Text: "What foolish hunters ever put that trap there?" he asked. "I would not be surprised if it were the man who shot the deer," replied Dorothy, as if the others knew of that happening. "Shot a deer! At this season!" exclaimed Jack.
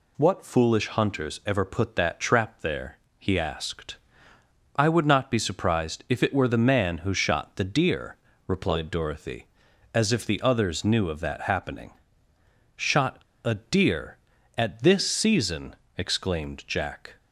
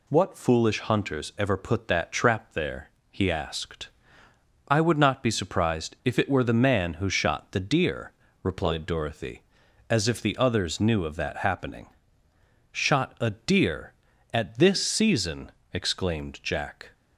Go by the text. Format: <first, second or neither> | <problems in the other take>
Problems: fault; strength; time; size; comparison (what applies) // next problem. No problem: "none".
second | pauses between "Shot" and "a"; slight; at 13.2 s; 0.21 s long